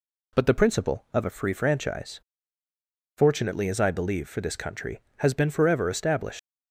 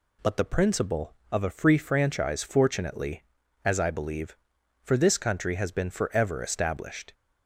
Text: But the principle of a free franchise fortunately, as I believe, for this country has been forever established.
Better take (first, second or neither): second